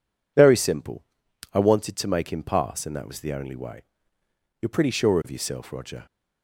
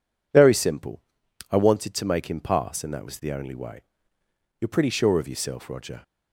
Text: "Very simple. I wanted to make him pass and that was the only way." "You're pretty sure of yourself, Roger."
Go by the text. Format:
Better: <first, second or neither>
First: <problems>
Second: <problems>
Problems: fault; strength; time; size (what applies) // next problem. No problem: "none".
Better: neither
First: none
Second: none